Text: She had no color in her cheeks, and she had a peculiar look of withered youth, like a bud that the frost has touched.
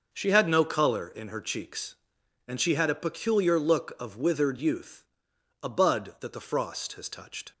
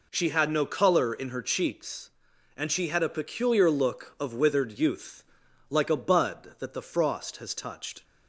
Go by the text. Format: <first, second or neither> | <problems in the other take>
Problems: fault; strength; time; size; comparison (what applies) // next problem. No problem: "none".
second | skips "like"; at 5.3 s